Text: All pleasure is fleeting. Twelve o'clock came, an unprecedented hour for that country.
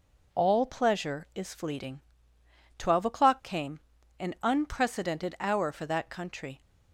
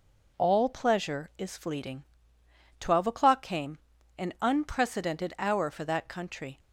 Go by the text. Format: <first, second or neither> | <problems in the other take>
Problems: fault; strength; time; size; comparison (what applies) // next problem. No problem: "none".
neither | none